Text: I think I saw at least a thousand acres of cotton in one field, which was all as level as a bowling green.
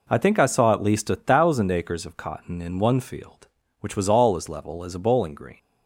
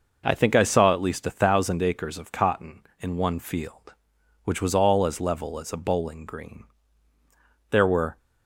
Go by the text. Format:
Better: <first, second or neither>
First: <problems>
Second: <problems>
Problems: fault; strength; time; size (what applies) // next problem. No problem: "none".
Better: first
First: none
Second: goes on to say "There were"; slight; from 7.6 s on; 0.48 s long